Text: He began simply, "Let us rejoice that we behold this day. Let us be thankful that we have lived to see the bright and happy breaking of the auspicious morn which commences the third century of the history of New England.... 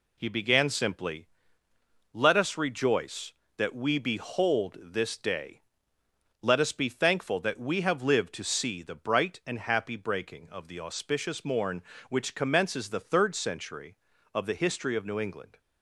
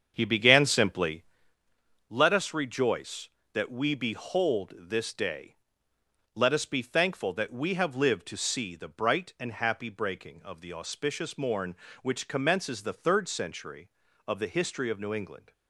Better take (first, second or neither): first